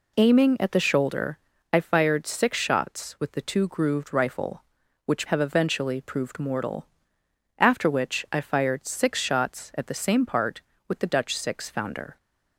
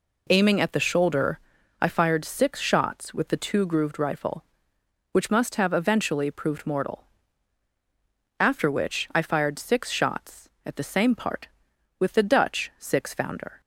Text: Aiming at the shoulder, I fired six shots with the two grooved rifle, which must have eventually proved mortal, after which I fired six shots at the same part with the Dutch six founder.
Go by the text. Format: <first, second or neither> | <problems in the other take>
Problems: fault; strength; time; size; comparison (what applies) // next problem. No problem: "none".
second | skips "must"; at 5.2 s